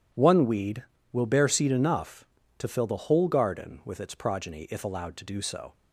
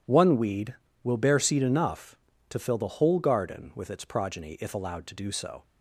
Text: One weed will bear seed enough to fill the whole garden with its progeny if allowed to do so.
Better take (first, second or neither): neither